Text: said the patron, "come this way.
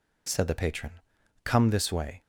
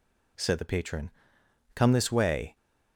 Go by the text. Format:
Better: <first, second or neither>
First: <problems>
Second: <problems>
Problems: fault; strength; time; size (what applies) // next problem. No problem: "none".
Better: neither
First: none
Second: none